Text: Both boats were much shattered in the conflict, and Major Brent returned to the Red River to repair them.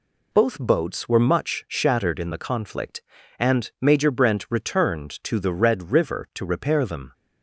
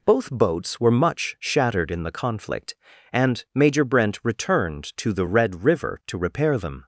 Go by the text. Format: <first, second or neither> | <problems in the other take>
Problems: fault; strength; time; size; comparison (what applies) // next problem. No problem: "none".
neither | none